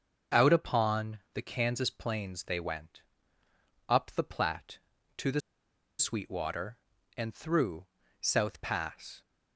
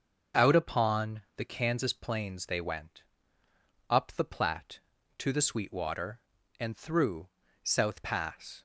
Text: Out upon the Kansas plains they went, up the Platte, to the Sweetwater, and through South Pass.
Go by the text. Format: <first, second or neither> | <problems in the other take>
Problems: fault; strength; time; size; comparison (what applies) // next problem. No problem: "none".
second | starts louder than the rest; until 1.4 s; 6.5 dB; also in the second // pauses between "upon" and "the"; slight; at 1.1 s; 0.16 s long; slight in the second // pauses between "the" and "Sweetwater"; noticeable; at 5.4 s; 0.58 s long // pauses between "through" and "South"; slight; at 7.8 s; 0.34 s long; slight in the second